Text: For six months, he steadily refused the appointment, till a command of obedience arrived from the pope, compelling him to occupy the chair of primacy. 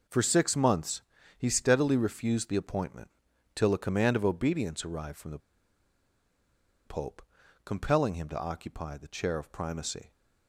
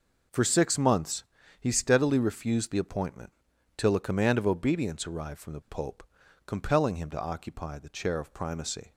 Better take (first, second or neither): second